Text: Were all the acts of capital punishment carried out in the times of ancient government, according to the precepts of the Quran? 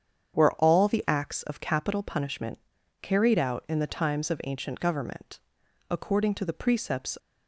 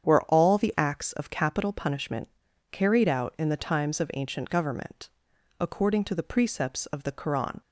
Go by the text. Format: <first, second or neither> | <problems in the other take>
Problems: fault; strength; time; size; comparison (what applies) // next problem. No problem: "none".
second | starts louder than the rest; strong; until 1.4 s; 8 dB; strong in the second // pauses between "punishment" and "carried"; at 2.5 s; 0.42 s long; also in the second // stops before "of the Quran"; at 7.1 s